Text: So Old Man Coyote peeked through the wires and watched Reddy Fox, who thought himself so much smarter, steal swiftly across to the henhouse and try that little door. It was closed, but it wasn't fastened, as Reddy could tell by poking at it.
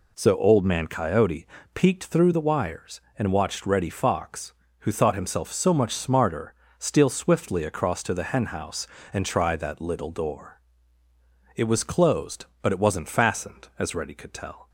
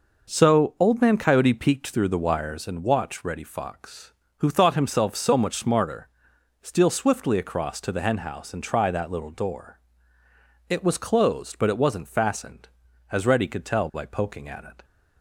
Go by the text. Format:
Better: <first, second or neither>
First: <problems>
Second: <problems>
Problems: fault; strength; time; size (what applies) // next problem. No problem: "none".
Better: second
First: pauses between "Coyote" and "peeked"; slight; at 1.4 s; 0.30 s long // stops before "by poking at it"; at 14.6 s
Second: none